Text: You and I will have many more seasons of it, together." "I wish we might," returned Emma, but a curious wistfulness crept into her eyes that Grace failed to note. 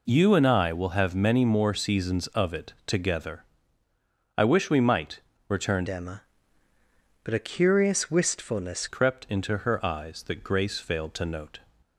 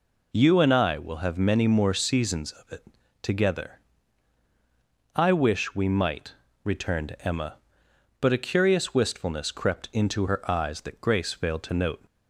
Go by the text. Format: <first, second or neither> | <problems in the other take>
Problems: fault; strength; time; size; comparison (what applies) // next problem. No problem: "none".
second | changes voice from "Emma" to "wistfulness"; from 5.8 to 8.8 s; 3.0 s long